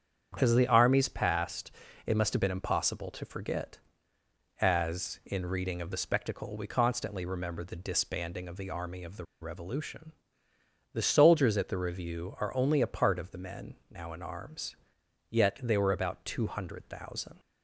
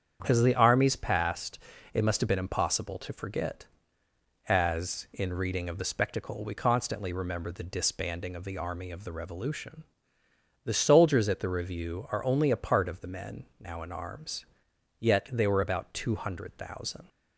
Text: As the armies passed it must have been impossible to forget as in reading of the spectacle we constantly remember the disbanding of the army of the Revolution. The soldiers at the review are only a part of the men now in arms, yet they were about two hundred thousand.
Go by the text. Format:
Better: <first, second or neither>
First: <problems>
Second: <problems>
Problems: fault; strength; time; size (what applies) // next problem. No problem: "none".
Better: second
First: starts louder than the rest; strong; until 1.4 s; 8 dB // pauses between "passed" and "it"; slight; at 1.7 s; 0.34 s long // pauses between "the" and "Revolution"; slight; at 9.2 s; 0.17 s long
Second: starts louder than the rest; strong; until 1.2 s; 8 dB // pauses between "passed" and "it"; slight; at 1.5 s; 0.34 s long